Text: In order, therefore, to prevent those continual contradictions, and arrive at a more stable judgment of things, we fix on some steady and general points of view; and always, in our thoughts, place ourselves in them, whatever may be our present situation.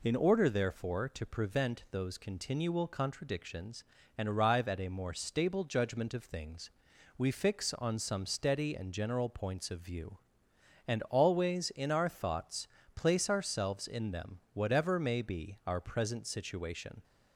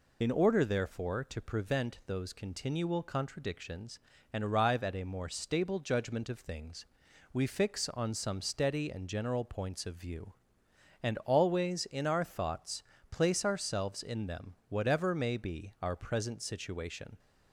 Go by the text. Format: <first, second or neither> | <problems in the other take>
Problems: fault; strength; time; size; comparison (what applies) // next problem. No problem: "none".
first | loses the start of "In"; at 0.2 s; 50 ms